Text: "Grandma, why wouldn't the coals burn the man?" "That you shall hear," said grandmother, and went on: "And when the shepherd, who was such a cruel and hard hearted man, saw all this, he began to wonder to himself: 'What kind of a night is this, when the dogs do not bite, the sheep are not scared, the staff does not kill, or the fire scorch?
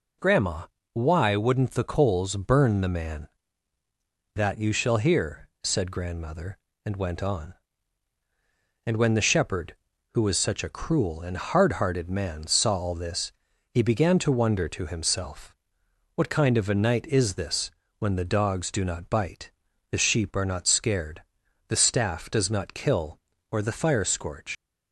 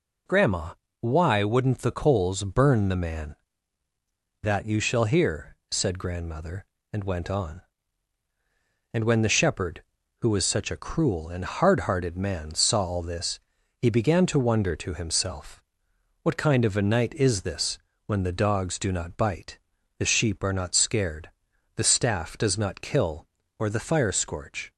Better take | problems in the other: second | leaves "scorch" unfinished; at 24.5 s; 90 ms

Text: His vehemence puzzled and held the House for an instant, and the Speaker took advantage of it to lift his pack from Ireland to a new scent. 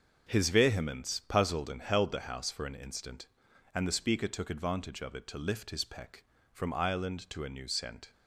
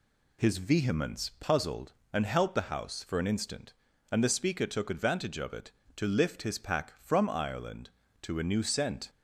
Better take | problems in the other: second | starts louder than the rest; until 1.3 s; 6.5 dB // says "peck" for "pack"; at 5.8 s

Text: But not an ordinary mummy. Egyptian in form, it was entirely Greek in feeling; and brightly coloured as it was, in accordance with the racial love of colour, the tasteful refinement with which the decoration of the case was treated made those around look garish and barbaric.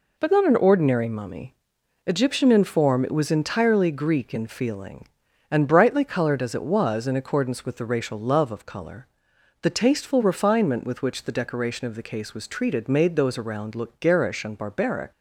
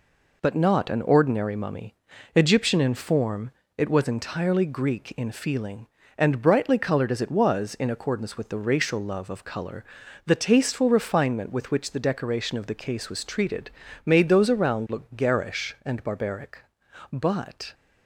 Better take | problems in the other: first | pauses between "treated" and "made"; slight; at 13.7 s; 0.34 s long // goes on to say "But"; noticeable; from 17.1 s on; 0.62 s long

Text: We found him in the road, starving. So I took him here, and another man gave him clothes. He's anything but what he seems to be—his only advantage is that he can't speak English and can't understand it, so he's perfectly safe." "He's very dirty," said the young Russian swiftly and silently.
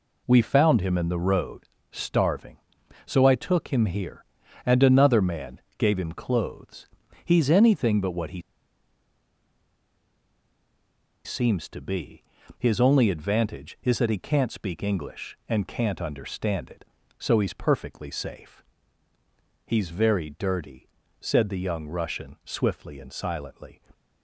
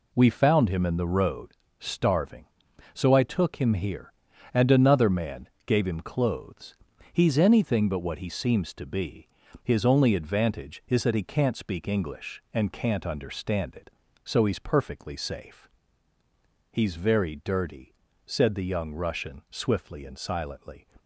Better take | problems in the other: second | pauses between "man" and "gave"; slight; at 5.5 s; 0.16 s long; slight in the second // pauses between "he" and "seems"; strong; at 8.3 s; 2.8 s long

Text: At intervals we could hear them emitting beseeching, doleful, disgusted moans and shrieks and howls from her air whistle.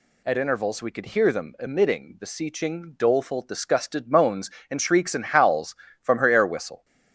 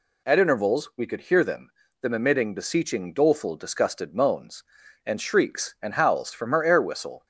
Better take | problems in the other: first | says "them" twice; at 2.0 s

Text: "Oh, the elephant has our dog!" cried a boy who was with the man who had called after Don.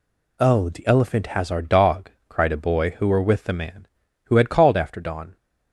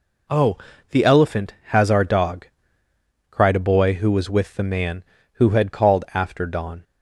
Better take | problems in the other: second | says "were" for "was"; at 3.0 s

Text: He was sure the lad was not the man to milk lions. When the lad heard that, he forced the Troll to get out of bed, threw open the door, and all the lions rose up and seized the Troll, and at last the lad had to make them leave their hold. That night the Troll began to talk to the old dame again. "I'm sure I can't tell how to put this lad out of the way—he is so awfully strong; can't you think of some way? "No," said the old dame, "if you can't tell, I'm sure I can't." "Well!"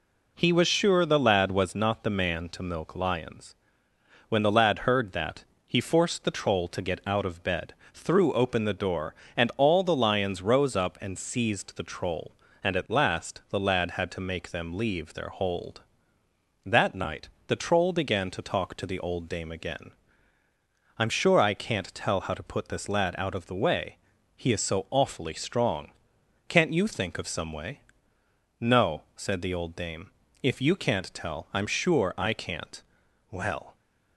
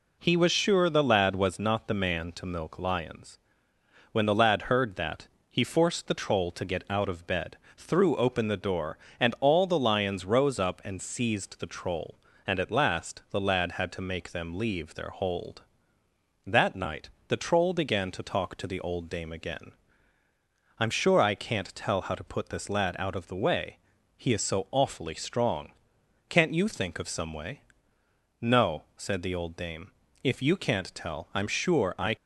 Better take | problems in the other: first | pauses between "night" and "the"; slight; at 17.1 s; 0.18 s long; slight in the first // stops before "can't Well"; at 32.1 s

